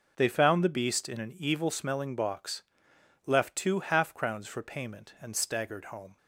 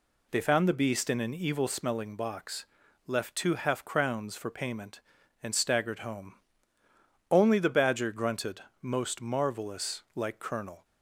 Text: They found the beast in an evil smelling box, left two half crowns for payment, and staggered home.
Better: first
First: none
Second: goes on to say "Only the badger grunted most marvelous like Colonel"; strong; from 7.3 s on; 3.5 s long

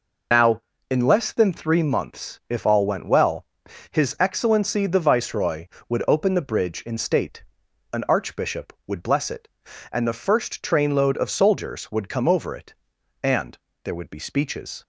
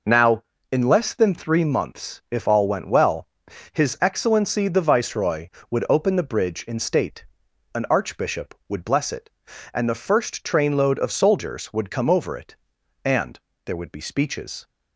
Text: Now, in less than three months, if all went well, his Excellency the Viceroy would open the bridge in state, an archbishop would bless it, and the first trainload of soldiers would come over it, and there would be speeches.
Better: second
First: loses the start of "Now"; at 0.3 s; 65 ms // pauses between "and" and "there"; slight; at 13.5 s; 0.26 s long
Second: pauses between "and" and "there"; slight; at 13.3 s; 0.26 s long

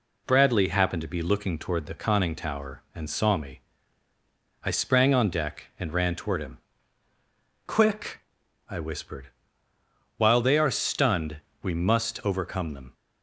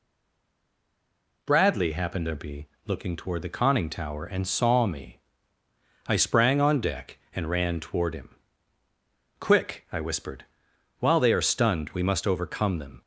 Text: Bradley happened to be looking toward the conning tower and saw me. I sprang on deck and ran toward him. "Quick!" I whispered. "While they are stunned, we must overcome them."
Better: first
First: none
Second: stays silent before the first word; noticeable; until 1.4 s; 1.4 s long // pauses between "be" and "looking"; slight; at 2.6 s; 0.18 s long

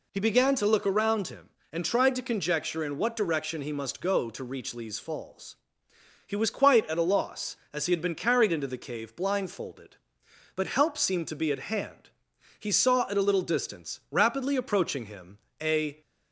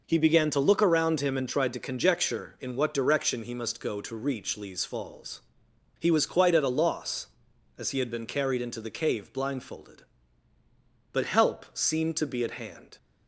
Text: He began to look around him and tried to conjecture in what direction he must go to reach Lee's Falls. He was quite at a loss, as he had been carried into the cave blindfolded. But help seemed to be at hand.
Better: second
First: goes on to say "He saw at a little distance rapidly approaching him a"; strong; from 12.5 s on; 3.4 s long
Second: none

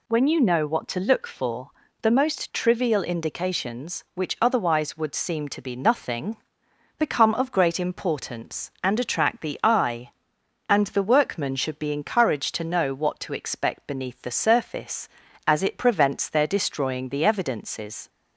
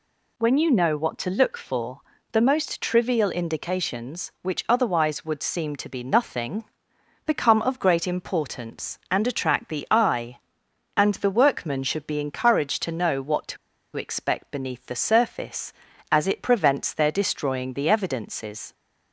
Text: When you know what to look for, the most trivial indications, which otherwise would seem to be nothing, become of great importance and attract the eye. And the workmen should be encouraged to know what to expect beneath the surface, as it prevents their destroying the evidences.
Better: first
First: none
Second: pauses between "to" and "expect"; at 13.5 s; 0.39 s long

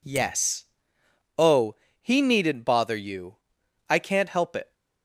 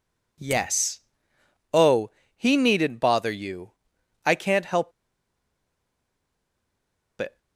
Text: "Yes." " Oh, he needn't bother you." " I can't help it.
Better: first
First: none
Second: pauses between "help" and "it"; strong; at 4.9 s; 2.2 s long

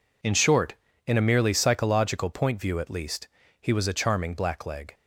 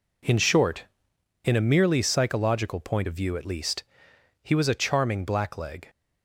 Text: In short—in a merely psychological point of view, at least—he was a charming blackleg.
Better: second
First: skips "of"; at 2.5 s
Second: none

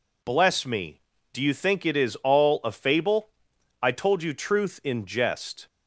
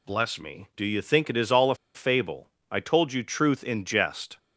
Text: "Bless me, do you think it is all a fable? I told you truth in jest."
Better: first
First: none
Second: pauses between "a" and "fable"; slight; at 1.7 s; 0.20 s long

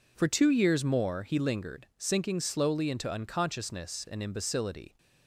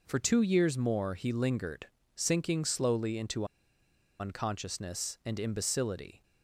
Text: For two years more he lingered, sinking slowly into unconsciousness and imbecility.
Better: first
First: none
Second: pauses between "into" and "unconsciousness"; noticeable; at 3.4 s; 0.75 s long

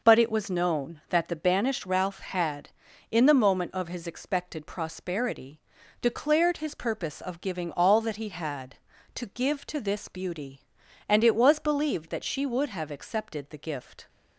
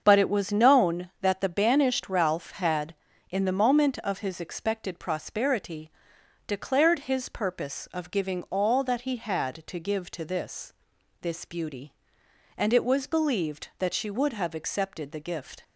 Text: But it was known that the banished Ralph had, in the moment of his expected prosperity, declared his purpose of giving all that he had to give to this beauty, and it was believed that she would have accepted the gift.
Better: first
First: none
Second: starts louder than the rest; until 1.0 s; 7 dB // says "this" twice; at 11.2 s

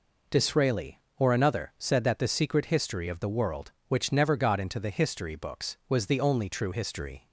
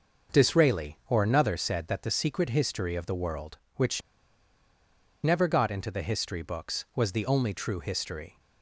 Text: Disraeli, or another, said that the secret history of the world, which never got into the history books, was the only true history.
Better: first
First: none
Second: starts louder than the rest; noticeable; until 1.4 s; 6 dB // pauses between "which" and "never"; at 4.0 s; 1.2 s long

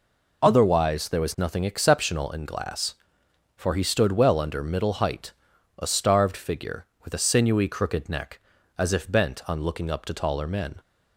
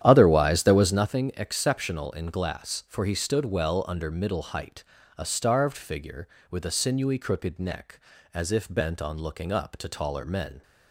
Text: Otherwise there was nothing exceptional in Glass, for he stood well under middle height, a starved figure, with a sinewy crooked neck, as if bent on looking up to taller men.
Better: first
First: none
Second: starts louder than the rest; strong; until 1.1 s; 10.5 dB

